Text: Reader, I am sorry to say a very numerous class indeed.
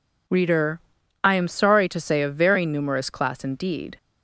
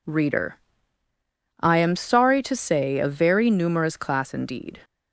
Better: neither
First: none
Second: none

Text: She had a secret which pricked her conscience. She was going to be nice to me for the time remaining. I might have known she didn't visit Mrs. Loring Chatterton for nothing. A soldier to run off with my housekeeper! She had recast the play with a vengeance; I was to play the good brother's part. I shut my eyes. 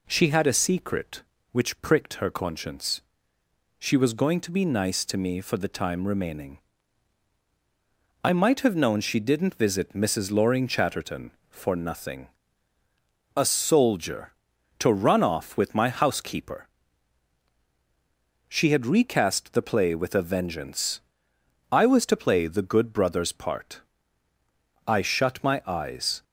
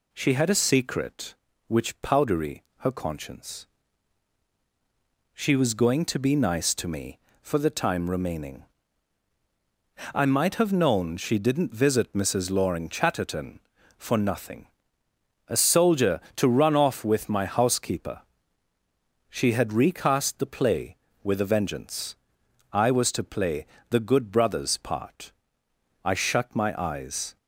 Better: first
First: none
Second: says "powdery" for "pricked"; at 2.0 s // pauses between "play" and "the"; slight; at 23.6 s; 0.24 s long

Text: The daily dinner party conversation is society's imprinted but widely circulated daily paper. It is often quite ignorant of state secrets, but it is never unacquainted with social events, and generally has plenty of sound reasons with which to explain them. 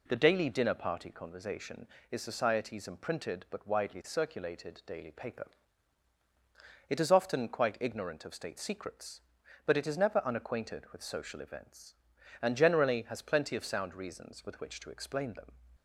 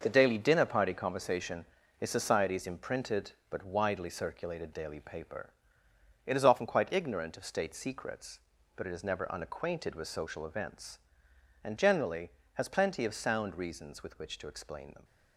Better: first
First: none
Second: gets quieter; strong; throughout; 8 dB

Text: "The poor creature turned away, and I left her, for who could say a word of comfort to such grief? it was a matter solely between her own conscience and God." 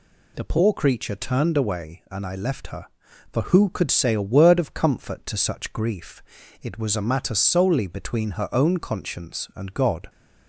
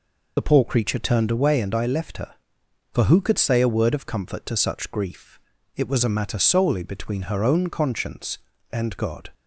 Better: first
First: none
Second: loses the start of "The"; at 0.3 s; 50 ms

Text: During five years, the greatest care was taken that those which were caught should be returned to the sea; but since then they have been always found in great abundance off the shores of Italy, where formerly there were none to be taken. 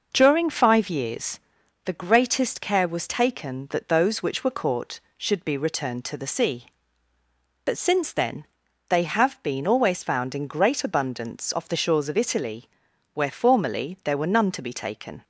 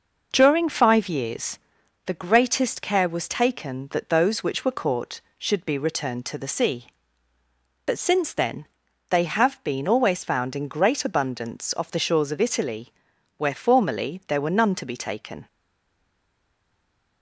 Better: first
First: pauses between "then" and "they"; noticeable; at 8.4 s; 0.46 s long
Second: pauses between "then" and "they"; noticeable; at 8.6 s; 0.46 s long // stays silent after the last word; noticeable; from 15.4 s on; 1.8 s long

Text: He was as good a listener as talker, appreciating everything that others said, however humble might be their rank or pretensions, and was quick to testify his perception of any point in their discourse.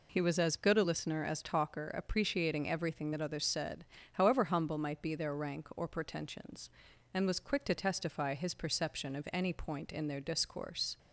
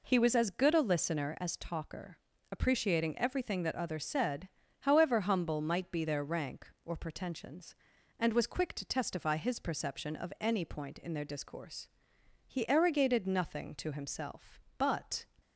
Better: first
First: none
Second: goes on to say "He arrogated nothing to himself but"; strong; from 12.4 s on; 2.8 s long

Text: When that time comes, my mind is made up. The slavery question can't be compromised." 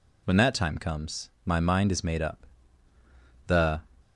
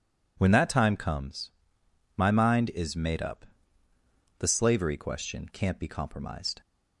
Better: second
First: stops before "slavery question can't be compromised"; at 4.0 s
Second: none

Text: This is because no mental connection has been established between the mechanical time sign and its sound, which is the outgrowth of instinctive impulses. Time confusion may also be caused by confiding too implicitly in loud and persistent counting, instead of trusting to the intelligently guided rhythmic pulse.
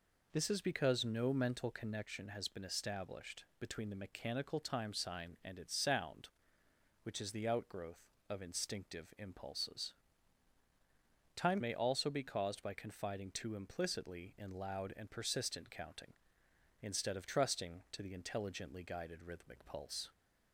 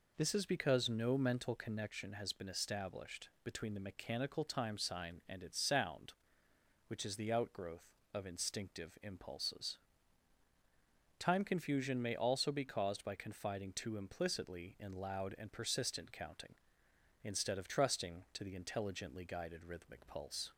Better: second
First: skips "confusion"; at 11.6 s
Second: none

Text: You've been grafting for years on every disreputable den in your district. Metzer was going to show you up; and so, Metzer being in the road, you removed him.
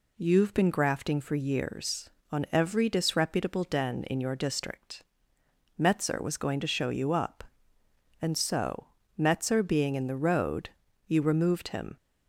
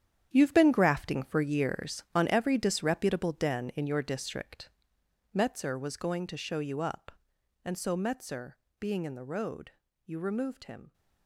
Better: first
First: none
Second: gets quieter; strong; throughout; 11.5 dB // pauses between "Metzer" and "being"; slight; at 8.5 s; 0.26 s long

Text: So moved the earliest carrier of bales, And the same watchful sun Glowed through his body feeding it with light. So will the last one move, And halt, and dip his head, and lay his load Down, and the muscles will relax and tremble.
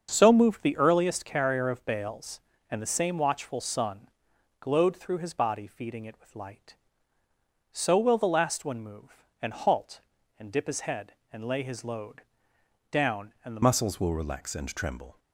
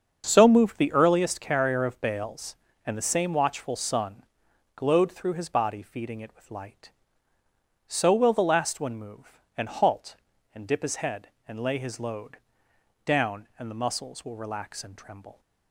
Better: second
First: starts louder than the rest; strong; until 1.1 s; 7 dB // pauses between "sun" and "Glowed"; noticeable; at 4.0 s; 0.52 s long // pauses between "load" and "Down"; noticeable; at 12.2 s; 0.68 s long // changes voice at "muscles"; from 13.6 s on; 1.5 s long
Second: starts louder than the rest; strong; until 1.2 s; 7 dB // pauses between "sun" and "Glowed"; noticeable; at 4.2 s; 0.52 s long // pauses between "load" and "Down"; noticeable; at 12.3 s; 0.66 s long

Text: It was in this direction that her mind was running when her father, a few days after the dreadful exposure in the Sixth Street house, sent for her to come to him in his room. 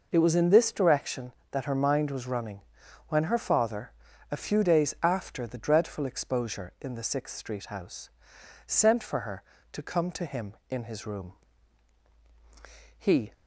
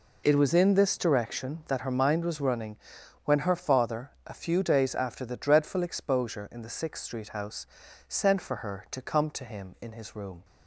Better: second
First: pauses between "running" and "when"; noticeable; at 2.6 s; 0.48 s long // goes on to say "He"; slight; from 12.9 s on; 0.36 s long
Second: pauses between "running" and "when"; noticeable; at 2.7 s; 0.48 s long

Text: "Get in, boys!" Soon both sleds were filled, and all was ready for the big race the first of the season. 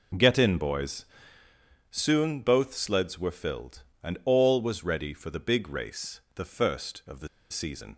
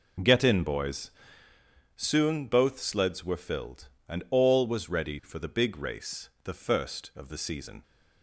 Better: second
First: pauses between "race" and "the"; slight; at 6.1 s; 0.16 s long // pauses between "the" and "season"; slight; at 7.2 s; 0.23 s long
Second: pauses between "race" and "the"; slight; at 6.2 s; 0.16 s long

